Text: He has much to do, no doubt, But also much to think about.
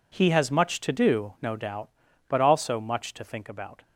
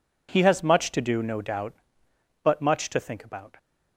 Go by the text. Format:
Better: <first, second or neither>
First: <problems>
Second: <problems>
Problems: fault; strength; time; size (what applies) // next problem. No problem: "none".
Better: first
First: none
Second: skips "also"; at 2.6 s